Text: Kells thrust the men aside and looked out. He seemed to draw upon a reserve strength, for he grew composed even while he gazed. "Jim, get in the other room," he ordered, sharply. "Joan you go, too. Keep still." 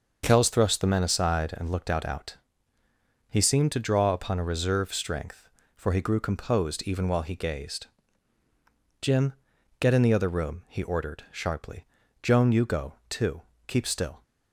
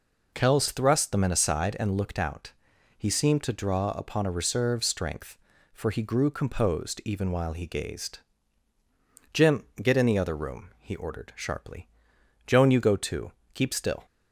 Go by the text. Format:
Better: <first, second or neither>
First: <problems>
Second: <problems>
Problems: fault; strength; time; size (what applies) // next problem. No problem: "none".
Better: second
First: starts louder than the rest; until 1.2 s; 6 dB // says "out" twice; at 2.0 s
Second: none